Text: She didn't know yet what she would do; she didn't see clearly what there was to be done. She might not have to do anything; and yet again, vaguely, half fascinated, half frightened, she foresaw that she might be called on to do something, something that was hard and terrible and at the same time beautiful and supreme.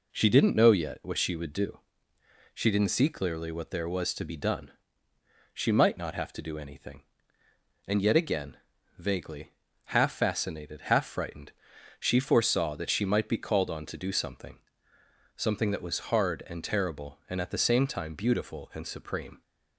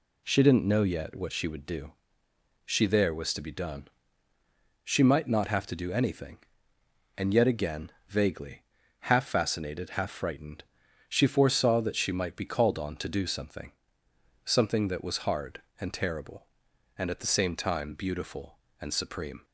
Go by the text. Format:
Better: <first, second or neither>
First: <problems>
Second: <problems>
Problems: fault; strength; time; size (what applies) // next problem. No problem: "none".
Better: first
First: none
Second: skips "didn't see clearly what"; at 2.8 s